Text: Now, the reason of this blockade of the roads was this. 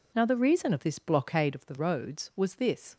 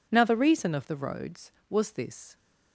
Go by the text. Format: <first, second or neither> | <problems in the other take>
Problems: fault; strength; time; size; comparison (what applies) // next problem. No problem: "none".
first | skips "this blockade of"; at 0.8 s